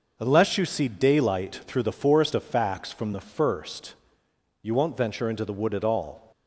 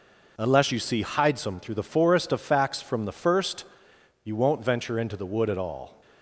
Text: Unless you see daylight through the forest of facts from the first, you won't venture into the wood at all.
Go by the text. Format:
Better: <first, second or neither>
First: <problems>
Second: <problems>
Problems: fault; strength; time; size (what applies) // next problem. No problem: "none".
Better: first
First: none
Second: says "hidesome" for "daylight"; at 1.0 s